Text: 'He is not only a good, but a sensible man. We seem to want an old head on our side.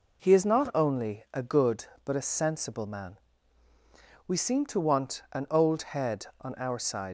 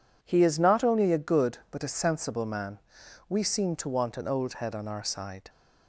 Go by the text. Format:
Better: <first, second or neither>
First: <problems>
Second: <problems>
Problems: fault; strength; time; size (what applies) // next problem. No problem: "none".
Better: second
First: pauses between "old" and "head"; slight; at 5.8 s; 0.16 s long // leaves "side" unfinished; at 7.0 s; 100 ms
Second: none